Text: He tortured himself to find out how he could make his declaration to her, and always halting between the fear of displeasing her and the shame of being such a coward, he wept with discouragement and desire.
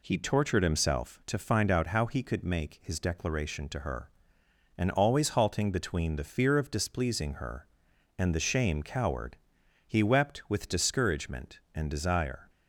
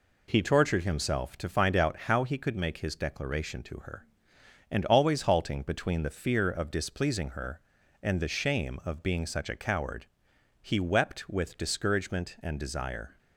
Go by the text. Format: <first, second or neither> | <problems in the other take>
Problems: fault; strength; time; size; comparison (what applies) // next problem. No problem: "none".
second | skips "of being such a"; at 8.8 s